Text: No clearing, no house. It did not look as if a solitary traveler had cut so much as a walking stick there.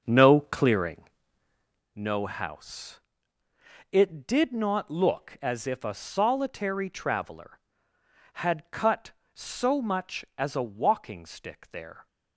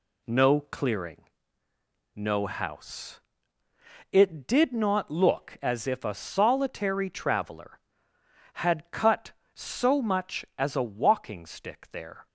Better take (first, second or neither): second